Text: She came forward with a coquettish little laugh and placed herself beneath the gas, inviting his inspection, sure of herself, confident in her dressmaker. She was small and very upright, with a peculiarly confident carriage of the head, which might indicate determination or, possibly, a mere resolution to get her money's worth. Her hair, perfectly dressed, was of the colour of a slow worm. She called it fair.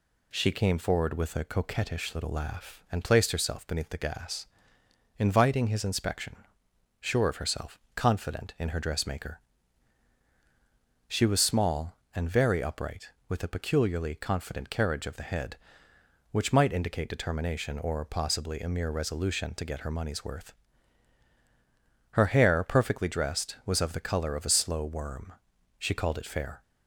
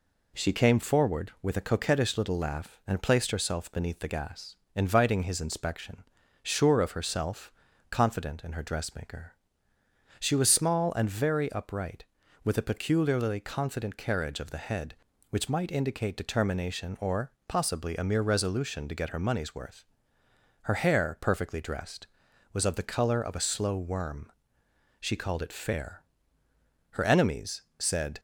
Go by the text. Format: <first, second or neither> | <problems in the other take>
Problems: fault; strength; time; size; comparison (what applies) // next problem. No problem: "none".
first | goes on to say "Her enemies said"; noticeable; from 26.9 s on; 1.2 s long